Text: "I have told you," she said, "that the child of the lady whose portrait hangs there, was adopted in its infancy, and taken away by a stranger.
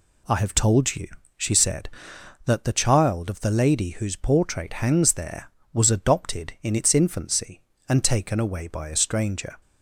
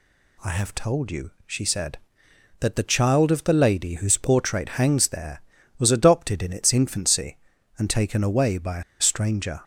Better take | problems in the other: first | pauses between "a" and "stranger"; slight; at 8.8 s; 0.18 s long

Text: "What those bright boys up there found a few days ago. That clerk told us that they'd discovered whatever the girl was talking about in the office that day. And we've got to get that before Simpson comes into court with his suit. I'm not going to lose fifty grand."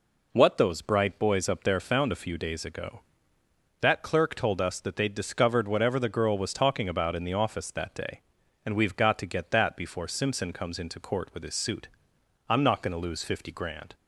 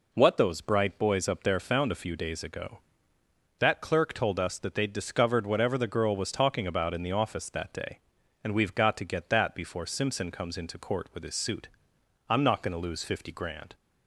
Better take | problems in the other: neither | none

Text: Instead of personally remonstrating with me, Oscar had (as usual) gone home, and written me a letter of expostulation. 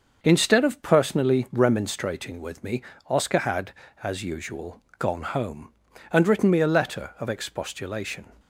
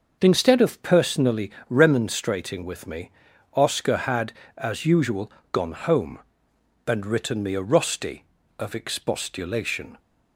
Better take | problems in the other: first | starts louder than the rest; noticeable; until 1.2 s; 6 dB; also in the first // pauses between "personally" and "remonstrating"; slight; at 1.5 s; 0.18 s long // says "rusty" for "letter"; at 7.6 s

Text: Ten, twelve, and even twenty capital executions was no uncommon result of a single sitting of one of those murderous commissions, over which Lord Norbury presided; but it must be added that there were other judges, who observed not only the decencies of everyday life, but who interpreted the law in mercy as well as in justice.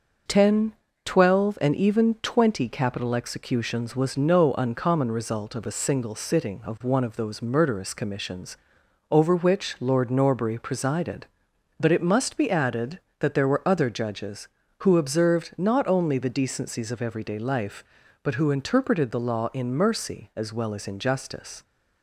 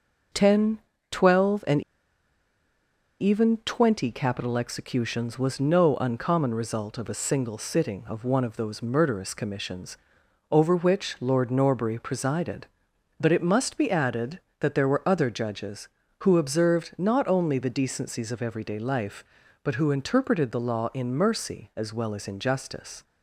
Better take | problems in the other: first | pauses between "and" and "even"; strong; at 1.7 s; 1.4 s long

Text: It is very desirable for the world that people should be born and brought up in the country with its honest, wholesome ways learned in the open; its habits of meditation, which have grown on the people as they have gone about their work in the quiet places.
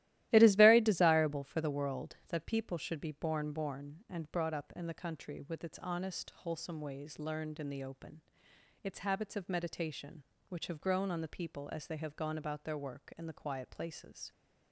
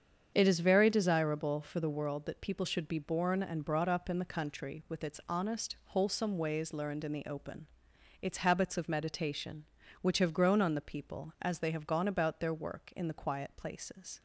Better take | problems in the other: second | starts louder than the rest; strong; until 1.3 s; 15 dB; strong in the second // says "born" twice; at 3.5 s

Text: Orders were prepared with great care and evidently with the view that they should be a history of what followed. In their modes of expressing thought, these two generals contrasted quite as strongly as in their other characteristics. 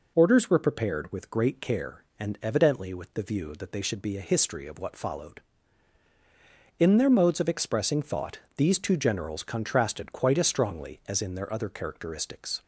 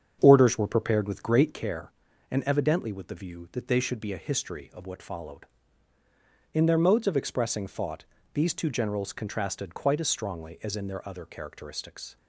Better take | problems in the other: first | starts louder than the rest; strong; until 1.8 s; 7.5 dB

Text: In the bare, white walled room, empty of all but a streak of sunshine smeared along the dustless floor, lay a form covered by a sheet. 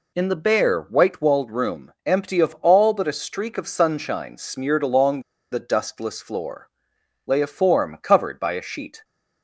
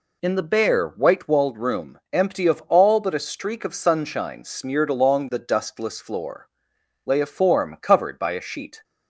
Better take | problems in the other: second | pauses between "along" and "the"; slight; at 5.2 s; 0.29 s long

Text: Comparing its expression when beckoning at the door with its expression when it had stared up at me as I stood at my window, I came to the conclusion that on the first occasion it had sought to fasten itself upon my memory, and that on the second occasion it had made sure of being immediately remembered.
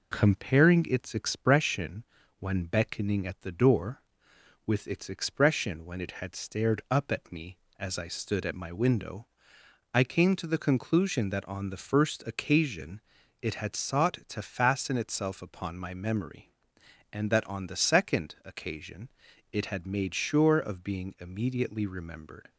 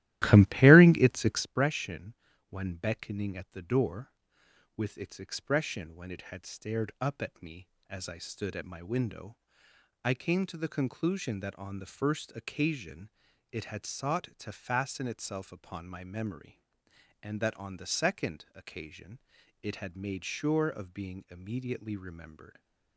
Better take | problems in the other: first | starts louder than the rest; strong; until 1.5 s; 15 dB // pauses between "expression" and "when"; slight; at 2.1 s; 0.34 s long; slight in the first // pauses between "occasion" and "it"; at 13.0 s; 0.42 s long; also in the first // pauses between "occasion" and "it"; noticeable; at 19.1 s; 0.46 s long; noticeable in the first

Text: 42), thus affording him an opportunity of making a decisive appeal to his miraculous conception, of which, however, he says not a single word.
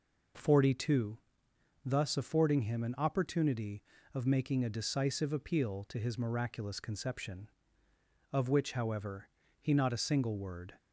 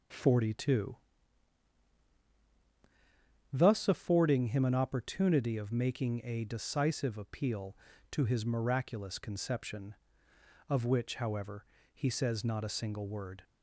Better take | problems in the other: second | skips "says"; at 9.7 s

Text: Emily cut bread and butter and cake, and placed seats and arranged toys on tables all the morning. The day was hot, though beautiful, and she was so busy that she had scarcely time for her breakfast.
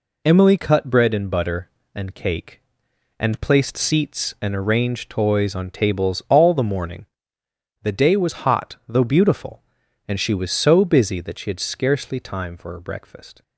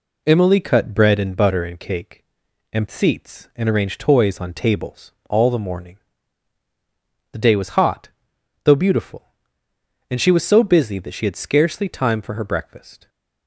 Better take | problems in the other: first | skips "placed"; at 2.8 s // pauses between "tables" and "all"; slight; at 5.1 s; 0.18 s long

